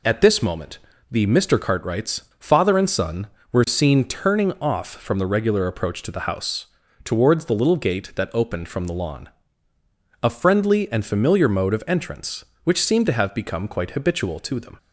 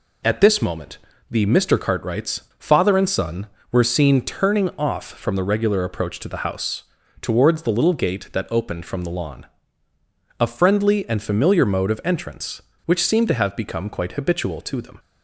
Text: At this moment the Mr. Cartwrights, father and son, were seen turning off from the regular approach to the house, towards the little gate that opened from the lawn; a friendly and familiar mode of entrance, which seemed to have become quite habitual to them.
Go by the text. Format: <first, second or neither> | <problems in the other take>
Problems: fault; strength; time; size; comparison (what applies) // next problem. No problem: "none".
neither | pauses between "moment" and "the"; slight; the same in both